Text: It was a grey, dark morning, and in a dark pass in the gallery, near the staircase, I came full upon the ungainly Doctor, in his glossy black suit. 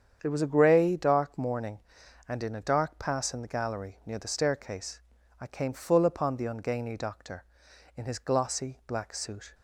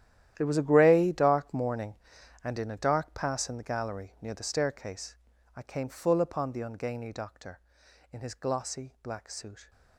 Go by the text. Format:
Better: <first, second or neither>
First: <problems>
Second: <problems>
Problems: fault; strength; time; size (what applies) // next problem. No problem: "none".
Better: first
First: starts louder than the rest; strong; until 1.2 s; 8 dB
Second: gets quieter; strong; throughout; 15.5 dB // starts louder than the rest; strong; until 1.3 s; 11.5 dB